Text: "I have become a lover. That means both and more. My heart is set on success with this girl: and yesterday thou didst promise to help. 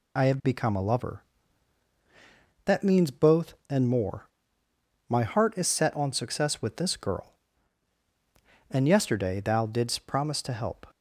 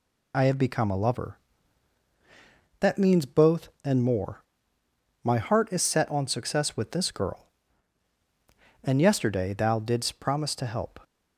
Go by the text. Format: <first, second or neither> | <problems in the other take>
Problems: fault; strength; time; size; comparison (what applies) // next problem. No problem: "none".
neither | none